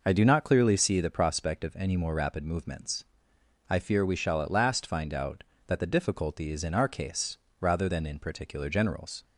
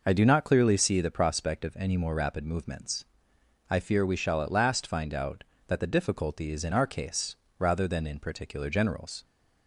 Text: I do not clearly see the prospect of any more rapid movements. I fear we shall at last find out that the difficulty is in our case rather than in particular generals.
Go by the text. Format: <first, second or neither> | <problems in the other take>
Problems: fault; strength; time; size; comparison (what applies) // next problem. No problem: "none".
neither | pauses between "case" and "rather"; slight; the same in both